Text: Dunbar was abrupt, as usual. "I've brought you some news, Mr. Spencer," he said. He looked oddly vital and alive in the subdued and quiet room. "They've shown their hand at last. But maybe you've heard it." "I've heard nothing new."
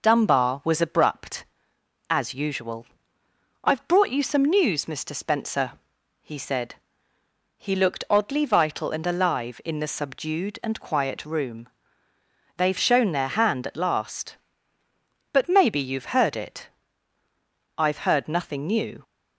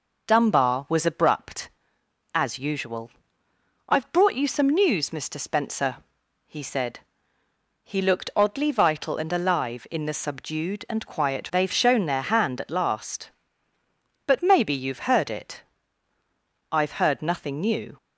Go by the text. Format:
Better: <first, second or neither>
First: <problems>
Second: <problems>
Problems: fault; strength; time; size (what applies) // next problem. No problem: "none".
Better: first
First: none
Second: skips "room"; at 11.5 s